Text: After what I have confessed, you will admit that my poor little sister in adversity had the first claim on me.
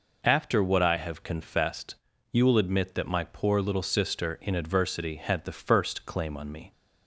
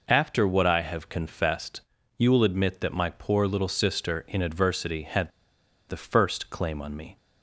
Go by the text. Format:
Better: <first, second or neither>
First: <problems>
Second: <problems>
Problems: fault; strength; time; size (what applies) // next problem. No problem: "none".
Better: first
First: none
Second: pauses between "had" and "the"; noticeable; at 5.3 s; 0.58 s long